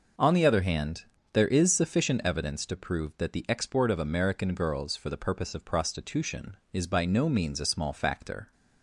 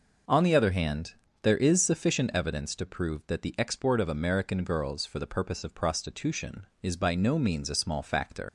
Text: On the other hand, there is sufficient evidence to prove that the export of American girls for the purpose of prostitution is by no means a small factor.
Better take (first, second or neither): first